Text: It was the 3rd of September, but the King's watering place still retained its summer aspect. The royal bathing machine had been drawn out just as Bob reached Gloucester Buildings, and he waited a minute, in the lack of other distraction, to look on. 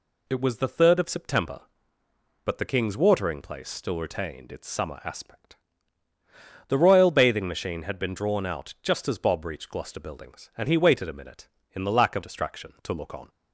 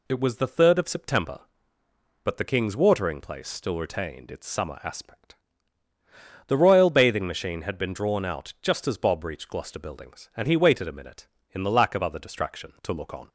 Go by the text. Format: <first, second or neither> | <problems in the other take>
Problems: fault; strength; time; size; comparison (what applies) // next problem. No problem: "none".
second | skips "other"; at 12.2 s